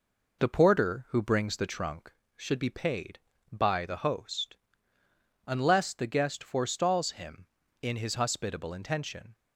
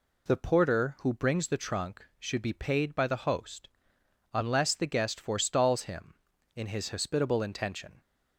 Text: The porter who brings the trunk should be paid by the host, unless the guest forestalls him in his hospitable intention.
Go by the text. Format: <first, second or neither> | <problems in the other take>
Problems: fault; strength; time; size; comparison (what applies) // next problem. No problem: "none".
second | starts louder than the rest; noticeable; until 2.2 s; 4.5 dB